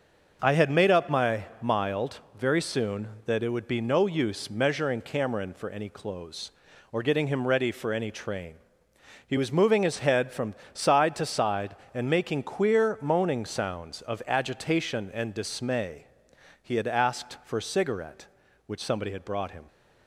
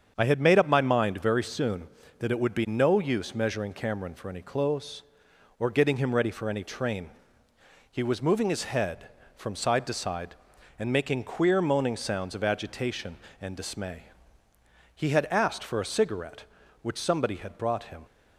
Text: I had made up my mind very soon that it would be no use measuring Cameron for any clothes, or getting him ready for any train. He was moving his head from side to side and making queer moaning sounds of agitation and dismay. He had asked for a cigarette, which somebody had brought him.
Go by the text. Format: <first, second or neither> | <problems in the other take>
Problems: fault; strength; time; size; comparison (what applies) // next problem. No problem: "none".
second | starts louder than the rest; until 1.4 s; 6.5 dB; strong in the second // says "mild" for "mind"; at 1.6 s // pauses between "from" and "side"; slight; at 10.5 s; 0.18 s long